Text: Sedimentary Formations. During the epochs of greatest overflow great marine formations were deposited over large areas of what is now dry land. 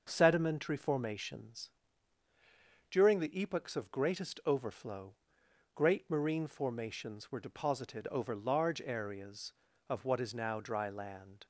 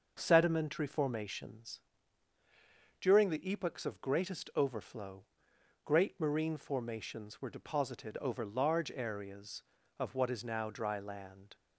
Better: neither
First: pauses between "overflow" and "great"; noticeable; at 5.1 s; 0.60 s long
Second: pauses between "overflow" and "great"; noticeable; at 5.2 s; 0.60 s long

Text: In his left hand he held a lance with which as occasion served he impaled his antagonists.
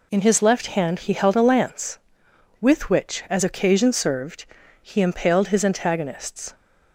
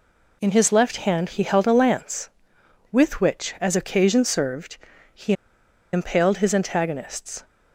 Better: first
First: pauses between "served" and "he"; slight; at 4.4 s; 0.36 s long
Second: pauses between "served" and "he"; slight; at 4.7 s; 0.36 s long // pauses between "he" and "impaled"; noticeable; at 5.3 s; 0.60 s long

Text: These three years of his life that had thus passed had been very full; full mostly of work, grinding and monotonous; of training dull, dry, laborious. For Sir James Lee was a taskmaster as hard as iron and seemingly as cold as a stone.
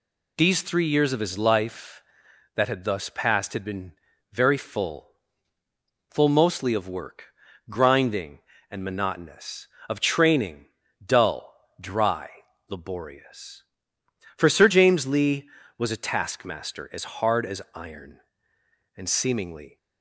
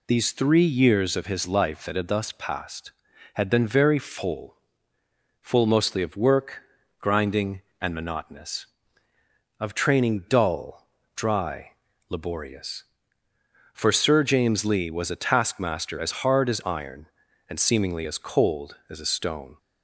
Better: second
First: pauses between "been" and "very"; at 3.9 s; 0.40 s long // pauses between "training" and "dull"; at 10.6 s; 0.36 s long // stops before "as cold as a stone"; at 19.7 s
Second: none

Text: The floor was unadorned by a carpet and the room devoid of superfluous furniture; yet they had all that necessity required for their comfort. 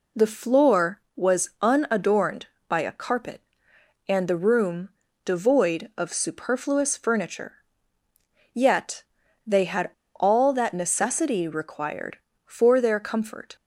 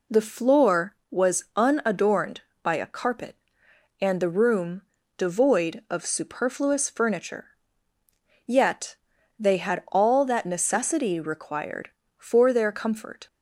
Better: second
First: pauses between "room" and "devoid"; slight; at 4.9 s; 0.34 s long // pauses between "yet" and "they"; at 9.0 s; 0.42 s long // pauses between "had" and "all"; slight; at 9.9 s; 0.24 s long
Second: pauses between "room" and "devoid"; slight; at 4.8 s; 0.34 s long // pauses between "yet" and "they"; at 8.9 s; 0.42 s long

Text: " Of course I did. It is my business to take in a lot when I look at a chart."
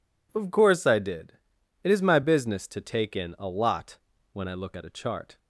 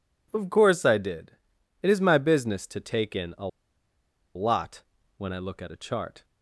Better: first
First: pauses between "lot" and "when"; slight; at 3.9 s; 0.34 s long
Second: pauses between "a" and "lot"; noticeable; at 3.4 s; 0.88 s long // pauses between "lot" and "when"; slight; at 4.8 s; 0.34 s long

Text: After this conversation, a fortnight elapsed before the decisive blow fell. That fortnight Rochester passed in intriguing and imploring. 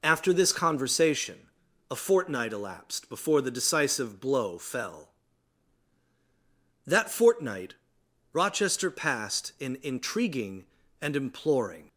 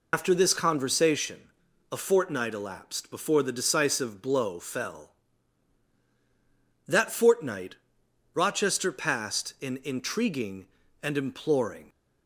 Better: first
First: pauses between "fortnight" and "Rochester"; noticeable; at 7.7 s; 0.58 s long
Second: loses the start of "After"; at 0.1 s; 85 ms // pauses between "fortnight" and "Rochester"; noticeable; at 7.7 s; 0.58 s long

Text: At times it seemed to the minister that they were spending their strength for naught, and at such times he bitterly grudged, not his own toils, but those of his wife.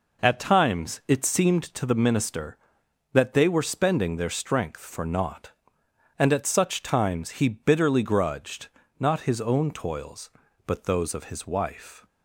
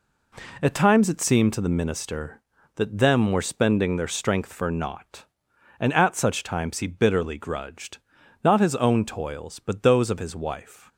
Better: first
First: none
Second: says "them" for "they"; at 2.9 s

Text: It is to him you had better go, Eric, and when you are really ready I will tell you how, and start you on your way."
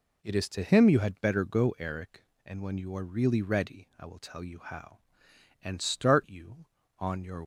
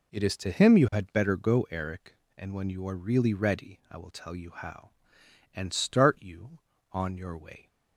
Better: second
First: stops before "way"; at 7.4 s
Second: none

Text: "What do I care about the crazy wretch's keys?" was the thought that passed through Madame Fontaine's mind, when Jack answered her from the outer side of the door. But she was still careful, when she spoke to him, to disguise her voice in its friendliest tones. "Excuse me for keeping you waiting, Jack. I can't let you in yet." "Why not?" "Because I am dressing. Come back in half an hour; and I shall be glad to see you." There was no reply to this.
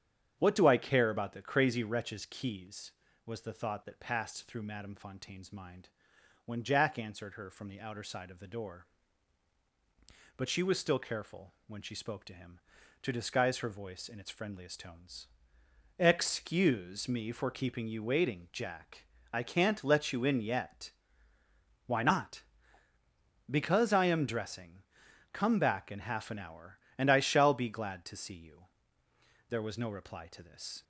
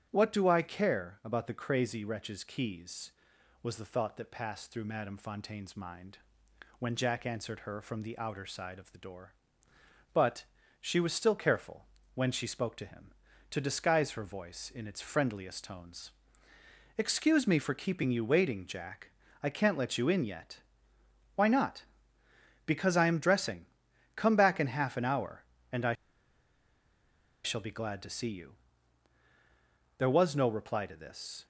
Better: first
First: starts louder than the rest; strong; until 1.4 s; 9 dB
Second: starts louder than the rest; strong; until 1.1 s; 10 dB // pauses between "But" and "she"; slight; at 10.4 s; 0.36 s long // pauses between "I" and "shall"; strong; at 25.9 s; 1.5 s long

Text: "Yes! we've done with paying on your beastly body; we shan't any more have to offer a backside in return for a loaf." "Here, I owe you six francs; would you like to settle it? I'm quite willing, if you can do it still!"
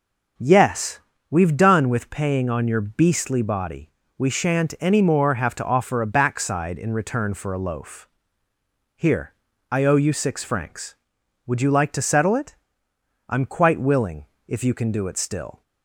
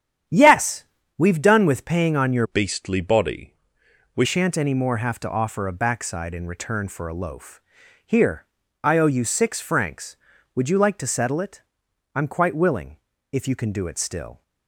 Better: first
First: none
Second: starts louder than the rest; strong; until 1.6 s; 9.5 dB // changes voice from "beastly" to "we"; from 2.4 to 4.2 s; 1.8 s long

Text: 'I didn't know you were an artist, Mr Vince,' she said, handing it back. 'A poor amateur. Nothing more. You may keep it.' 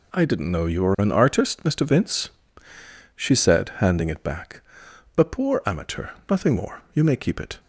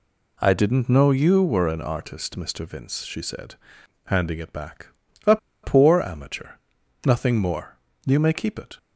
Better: first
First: none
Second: pauses between "A" and "poor"; slight; at 5.3 s; 0.25 s long

